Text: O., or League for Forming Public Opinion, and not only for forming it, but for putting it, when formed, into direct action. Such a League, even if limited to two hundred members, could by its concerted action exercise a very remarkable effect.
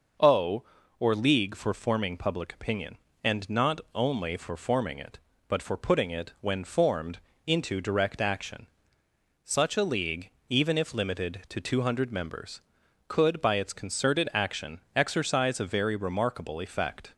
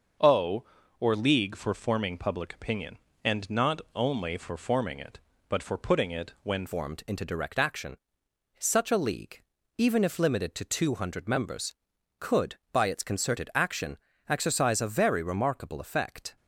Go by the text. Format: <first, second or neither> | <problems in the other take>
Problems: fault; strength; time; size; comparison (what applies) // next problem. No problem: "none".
first | changes voice at "formed"; from 6.6 s on; 9.7 s long // pauses between "action" and "exercise"; slight; at 13.9 s; 0.32 s long; slight in the first